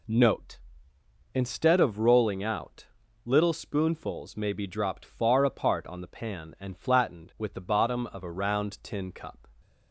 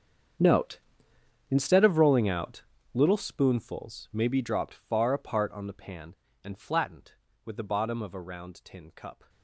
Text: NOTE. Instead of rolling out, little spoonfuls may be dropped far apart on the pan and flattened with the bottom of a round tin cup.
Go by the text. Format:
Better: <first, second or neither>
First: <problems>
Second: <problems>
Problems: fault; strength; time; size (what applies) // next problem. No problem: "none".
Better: first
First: none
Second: gets quieter; strong; throughout; 18 dB